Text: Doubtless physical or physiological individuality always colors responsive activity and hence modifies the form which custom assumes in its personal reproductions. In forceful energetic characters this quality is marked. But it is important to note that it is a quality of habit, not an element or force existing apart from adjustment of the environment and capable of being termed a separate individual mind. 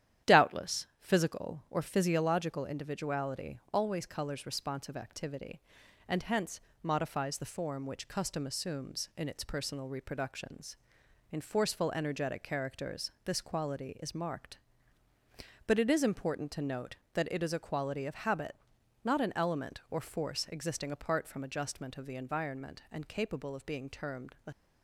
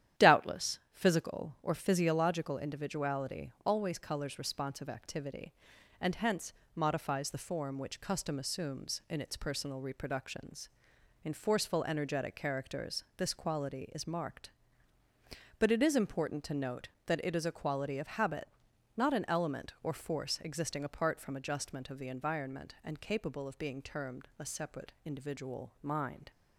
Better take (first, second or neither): second